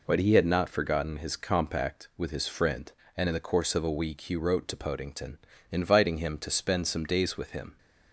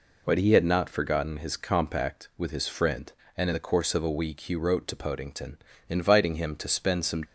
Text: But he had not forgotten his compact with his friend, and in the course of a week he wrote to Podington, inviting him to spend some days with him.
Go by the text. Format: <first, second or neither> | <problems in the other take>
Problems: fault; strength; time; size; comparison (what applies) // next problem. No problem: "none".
first | stops before "days with him"; at 7.2 s